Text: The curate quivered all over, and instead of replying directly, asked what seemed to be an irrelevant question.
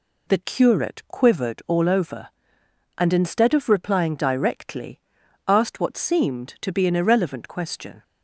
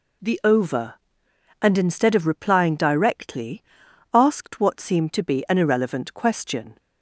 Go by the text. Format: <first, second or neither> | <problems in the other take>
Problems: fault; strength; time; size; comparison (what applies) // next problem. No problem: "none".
first | skips "curate quivered all"; at 0.4 s